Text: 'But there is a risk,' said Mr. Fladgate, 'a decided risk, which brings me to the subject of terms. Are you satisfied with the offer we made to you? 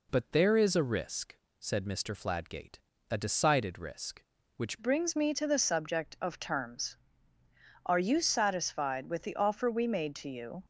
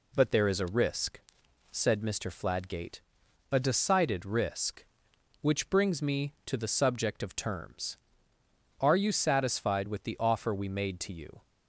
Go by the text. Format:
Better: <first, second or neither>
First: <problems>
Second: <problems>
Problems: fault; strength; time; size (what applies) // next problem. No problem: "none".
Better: second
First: changes voice at "brings"; from 4.8 s on; 5.8 s long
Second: none